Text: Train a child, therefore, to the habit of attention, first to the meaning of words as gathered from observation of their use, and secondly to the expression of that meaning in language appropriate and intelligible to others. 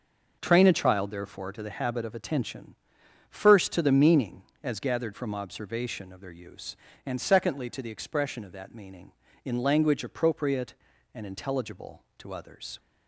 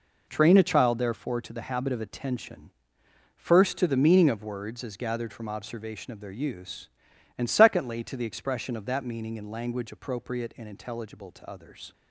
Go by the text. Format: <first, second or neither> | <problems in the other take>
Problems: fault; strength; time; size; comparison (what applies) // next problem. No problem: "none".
second | starts louder than the rest; noticeable; until 1.4 s; 6 dB // skips "of words"; at 4.5 s